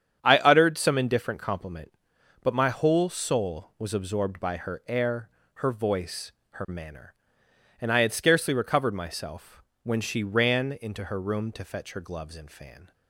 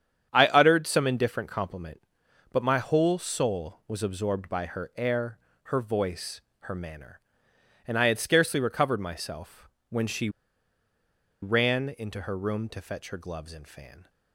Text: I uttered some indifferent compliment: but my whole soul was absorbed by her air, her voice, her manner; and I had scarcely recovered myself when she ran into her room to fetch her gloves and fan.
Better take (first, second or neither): first